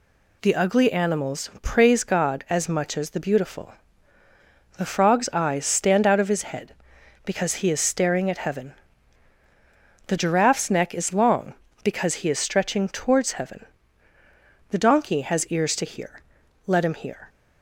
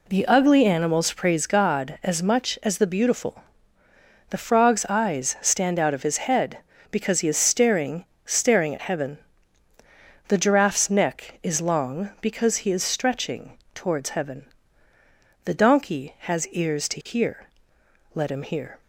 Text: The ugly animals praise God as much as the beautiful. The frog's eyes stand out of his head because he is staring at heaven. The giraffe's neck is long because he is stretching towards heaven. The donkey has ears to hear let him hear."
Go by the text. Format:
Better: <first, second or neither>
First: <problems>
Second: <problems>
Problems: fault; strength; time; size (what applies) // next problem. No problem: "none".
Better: first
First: pauses between "hear" and "let"; noticeable; at 16.2 s; 0.46 s long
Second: says "staring" twice; at 8.2 s // pauses between "stretching" and "towards"; slight; at 13.5 s; 0.18 s long // pauses between "hear" and "let"; noticeable; at 17.4 s; 0.66 s long